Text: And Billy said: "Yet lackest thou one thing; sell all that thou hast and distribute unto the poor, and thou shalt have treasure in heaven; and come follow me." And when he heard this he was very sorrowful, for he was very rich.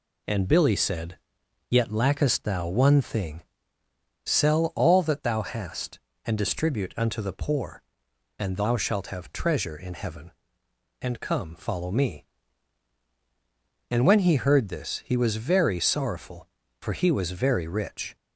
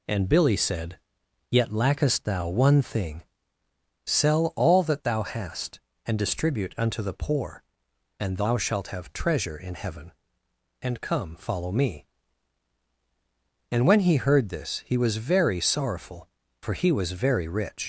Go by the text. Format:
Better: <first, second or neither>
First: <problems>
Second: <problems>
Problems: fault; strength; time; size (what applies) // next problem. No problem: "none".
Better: first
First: none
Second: leaves "rich" unfinished; at 17.8 s; 75 ms